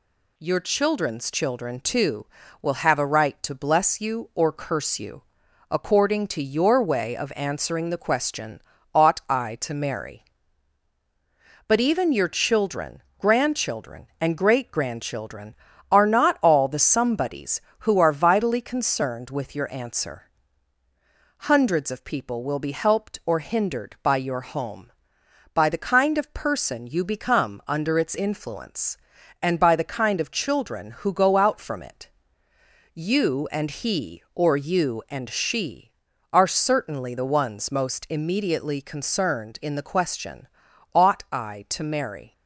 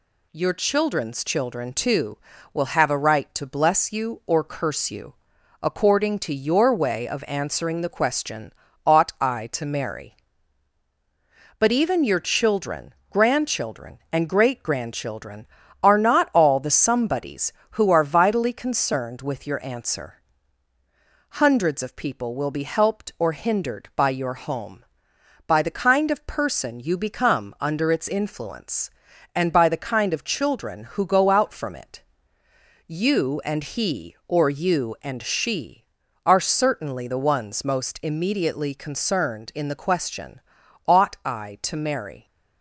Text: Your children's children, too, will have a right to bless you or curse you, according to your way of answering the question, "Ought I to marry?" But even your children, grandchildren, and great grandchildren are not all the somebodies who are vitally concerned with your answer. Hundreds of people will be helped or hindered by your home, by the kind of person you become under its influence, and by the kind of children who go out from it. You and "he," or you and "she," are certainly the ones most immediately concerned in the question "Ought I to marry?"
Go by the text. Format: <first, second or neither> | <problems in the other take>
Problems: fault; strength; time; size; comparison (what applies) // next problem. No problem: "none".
neither | pauses between "question" and "Ought"; noticeable; the same in both